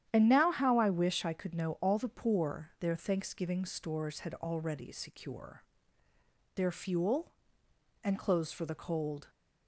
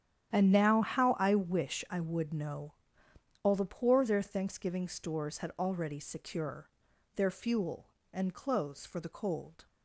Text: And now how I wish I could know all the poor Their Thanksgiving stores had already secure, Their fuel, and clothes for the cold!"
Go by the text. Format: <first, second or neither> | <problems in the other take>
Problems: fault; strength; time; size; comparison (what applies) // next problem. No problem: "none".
first | starts louder than the rest; strong; until 1.3 s; 10 dB; strong in the first // says "would" for "could"; at 1.9 s // pauses between "know" and "all"; noticeable; at 2.7 s; 0.70 s long